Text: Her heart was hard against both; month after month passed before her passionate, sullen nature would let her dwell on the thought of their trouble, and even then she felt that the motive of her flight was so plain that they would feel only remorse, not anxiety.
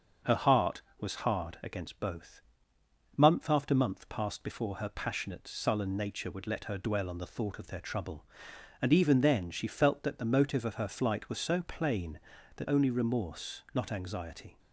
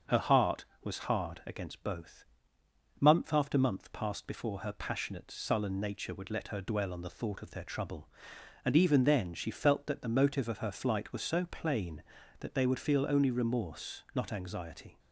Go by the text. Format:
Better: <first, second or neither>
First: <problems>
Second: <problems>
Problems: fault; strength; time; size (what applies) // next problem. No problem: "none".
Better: second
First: starts louder than the rest; until 1.4 s; 6.5 dB // skips "they would feel"; at 12.6 s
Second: starts louder than the rest; until 1.2 s; 6.5 dB